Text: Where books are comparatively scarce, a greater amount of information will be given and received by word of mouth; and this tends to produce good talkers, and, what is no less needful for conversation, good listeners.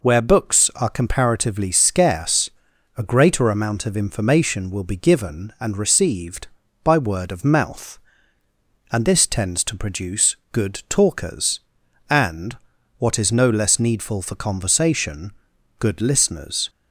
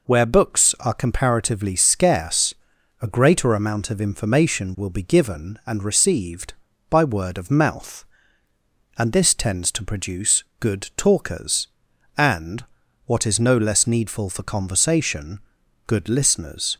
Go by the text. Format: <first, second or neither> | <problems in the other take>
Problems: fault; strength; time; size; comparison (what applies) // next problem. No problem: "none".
neither | pauses between "produce" and "good"; slight; the same in both